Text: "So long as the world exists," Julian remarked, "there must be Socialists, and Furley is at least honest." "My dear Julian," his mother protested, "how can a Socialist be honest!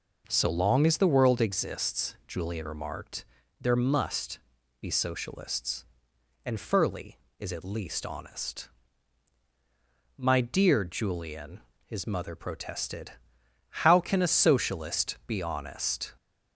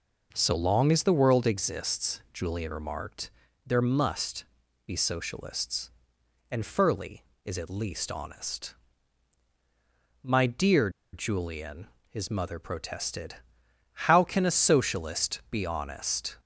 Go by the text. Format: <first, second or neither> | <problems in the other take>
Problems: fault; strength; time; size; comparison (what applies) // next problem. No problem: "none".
first | pauses between "must" and "be"; at 4.4 s; 0.40 s long; also in the first // pauses between "dear" and "Julian"; slight; at 10.8 s; 0.23 s long